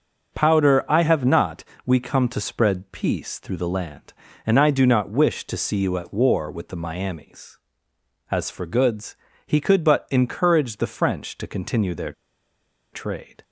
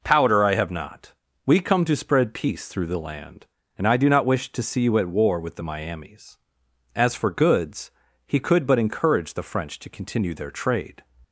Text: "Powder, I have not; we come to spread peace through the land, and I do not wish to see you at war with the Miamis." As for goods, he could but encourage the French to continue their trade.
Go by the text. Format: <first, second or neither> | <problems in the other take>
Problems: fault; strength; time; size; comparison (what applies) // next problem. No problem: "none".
second | starts louder than the rest; noticeable; until 1.4 s; 6 dB // pauses between "their" and "trade"; noticeable; at 12.1 s; 0.79 s long